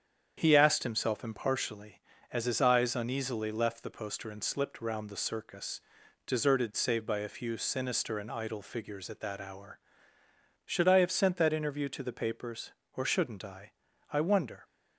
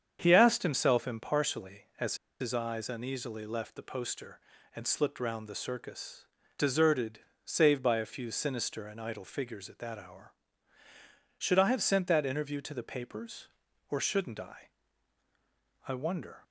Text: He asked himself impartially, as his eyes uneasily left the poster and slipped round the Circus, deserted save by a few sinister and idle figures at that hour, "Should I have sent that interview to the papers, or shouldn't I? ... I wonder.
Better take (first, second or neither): first